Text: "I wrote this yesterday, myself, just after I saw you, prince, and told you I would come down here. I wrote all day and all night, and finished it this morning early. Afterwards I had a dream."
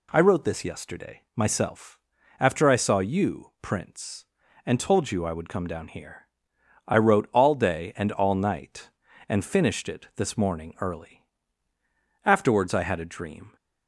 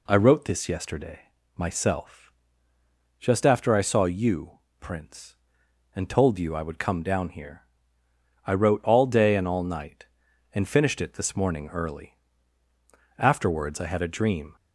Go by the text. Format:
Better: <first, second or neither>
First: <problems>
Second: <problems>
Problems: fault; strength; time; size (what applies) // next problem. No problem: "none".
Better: second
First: skips "just"; at 2.1 s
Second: none